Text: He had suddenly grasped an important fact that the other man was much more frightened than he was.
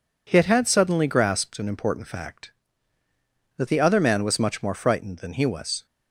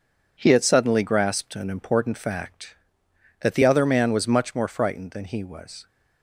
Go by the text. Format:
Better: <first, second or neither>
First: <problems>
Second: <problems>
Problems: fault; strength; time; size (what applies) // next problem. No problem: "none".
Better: second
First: says "had" twice; at 0.4 s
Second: none